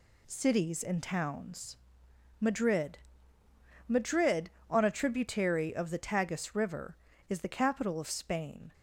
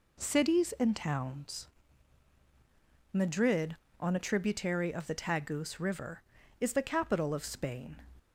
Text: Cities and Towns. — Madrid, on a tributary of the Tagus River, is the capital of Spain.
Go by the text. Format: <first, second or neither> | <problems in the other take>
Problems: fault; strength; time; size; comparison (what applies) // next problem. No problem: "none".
second | says "Madrid" twice; at 3.8 s